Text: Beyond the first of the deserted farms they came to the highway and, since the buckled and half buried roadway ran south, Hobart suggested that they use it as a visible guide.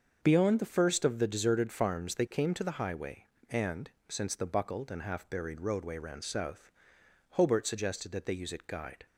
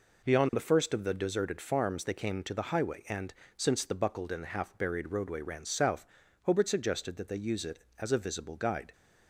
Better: second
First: starts louder than the rest; until 1.2 s; 6.5 dB // skips "as a visible"; at 8.6 s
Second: none

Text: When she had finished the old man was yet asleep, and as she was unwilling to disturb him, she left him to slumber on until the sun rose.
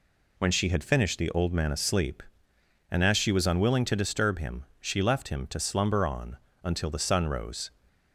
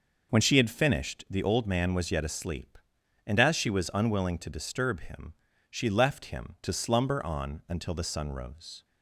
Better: second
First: skips "was yet"; at 1.7 s // pauses between "on" and "until"; slight; at 6.3 s; 0.26 s long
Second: none

